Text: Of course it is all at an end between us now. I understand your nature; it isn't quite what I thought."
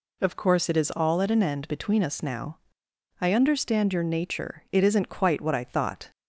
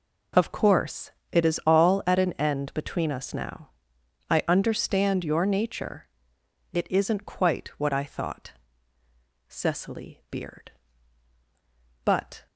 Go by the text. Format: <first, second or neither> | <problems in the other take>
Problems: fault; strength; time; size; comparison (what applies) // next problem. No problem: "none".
first | pauses between "course" and "it"; slight; at 1.1 s; 0.18 s long // goes on to say "Cecily beard but"; strong; from 9.4 s on; 3.0 s long